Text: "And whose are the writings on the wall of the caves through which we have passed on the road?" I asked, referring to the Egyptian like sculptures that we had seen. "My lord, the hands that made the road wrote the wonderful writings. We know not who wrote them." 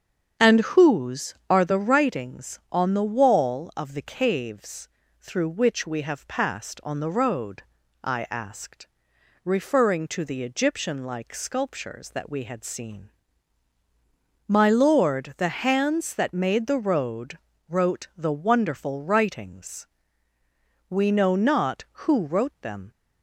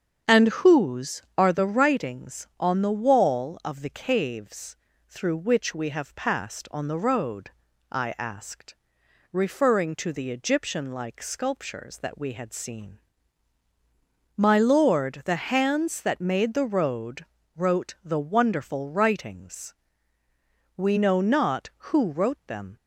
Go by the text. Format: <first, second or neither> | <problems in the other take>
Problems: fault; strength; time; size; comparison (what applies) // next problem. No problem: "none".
neither | starts louder than the rest; strong; the same in both // pauses between "caves" and "through"; slight; the same in both // pauses between "road" and "wrote"; slight; the same in both